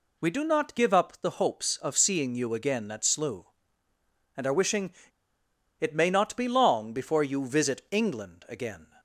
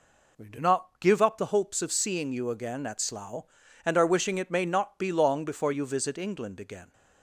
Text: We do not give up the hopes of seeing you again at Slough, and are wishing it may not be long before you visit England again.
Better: second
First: pauses between "wishing" and "it"; noticeable; at 4.9 s; 0.87 s long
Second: none

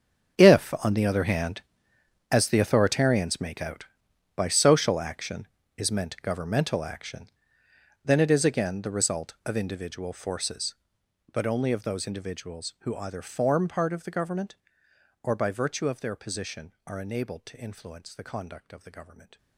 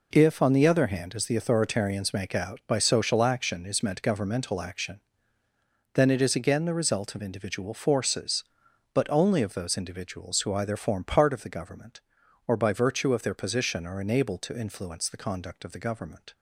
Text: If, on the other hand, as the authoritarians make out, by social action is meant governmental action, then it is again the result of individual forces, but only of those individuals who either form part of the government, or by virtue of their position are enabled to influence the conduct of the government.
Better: second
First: gets quieter; strong; throughout; 16.5 dB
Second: none

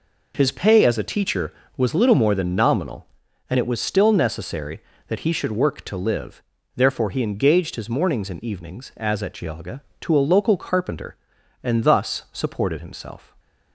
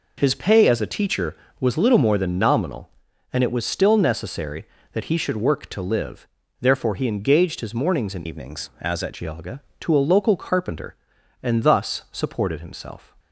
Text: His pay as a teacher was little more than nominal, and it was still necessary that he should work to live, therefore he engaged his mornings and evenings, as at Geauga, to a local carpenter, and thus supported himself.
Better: first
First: none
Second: changes voice from "evenings" to "at"; from 8.2 to 9.1 s; 0.9 s long

